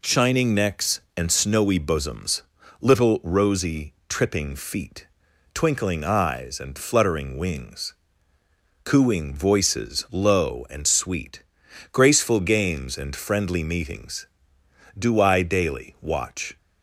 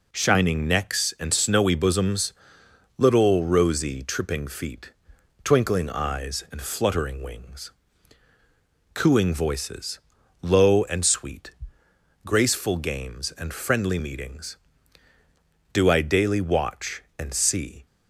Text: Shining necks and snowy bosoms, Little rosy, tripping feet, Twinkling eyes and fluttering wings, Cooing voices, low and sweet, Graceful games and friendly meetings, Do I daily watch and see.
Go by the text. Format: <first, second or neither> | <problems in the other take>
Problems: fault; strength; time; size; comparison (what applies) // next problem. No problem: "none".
second | stops before "and see"; at 16.5 s